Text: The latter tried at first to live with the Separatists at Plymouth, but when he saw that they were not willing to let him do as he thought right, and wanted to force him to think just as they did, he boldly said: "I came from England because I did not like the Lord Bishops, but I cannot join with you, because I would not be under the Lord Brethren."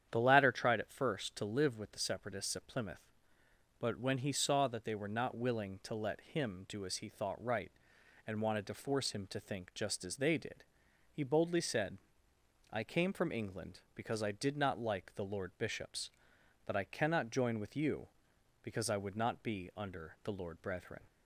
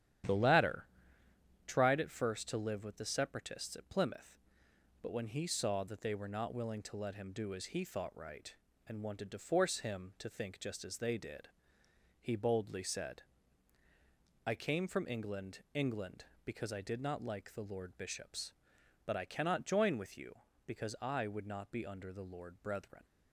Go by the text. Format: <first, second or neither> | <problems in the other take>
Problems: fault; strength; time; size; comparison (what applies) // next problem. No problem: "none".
first | starts louder than the rest; strong; until 2.0 s; 10.5 dB; strong in the first // pauses between "latter" and "tried"; noticeable; at 0.8 s; 0.80 s long // says "England" twice; at 15.7 s